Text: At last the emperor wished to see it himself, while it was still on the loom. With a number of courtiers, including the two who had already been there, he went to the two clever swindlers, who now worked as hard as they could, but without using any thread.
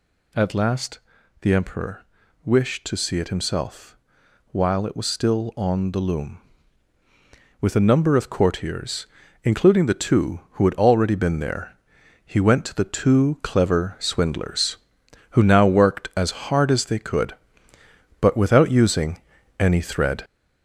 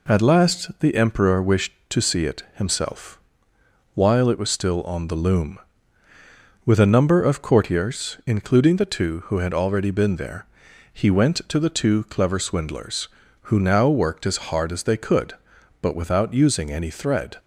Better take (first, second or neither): second